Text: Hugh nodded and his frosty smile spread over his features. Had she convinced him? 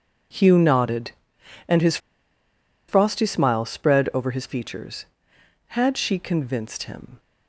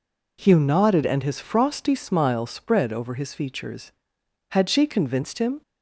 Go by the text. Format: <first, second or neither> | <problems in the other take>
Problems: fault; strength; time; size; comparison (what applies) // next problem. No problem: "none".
second | pauses between "his" and "frosty"; noticeable; at 1.9 s; 0.90 s long